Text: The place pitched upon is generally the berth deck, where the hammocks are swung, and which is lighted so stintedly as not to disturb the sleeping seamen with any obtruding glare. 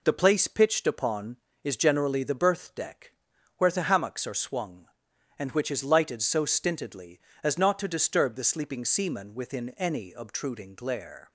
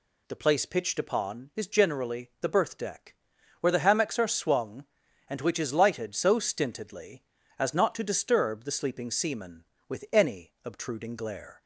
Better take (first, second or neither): second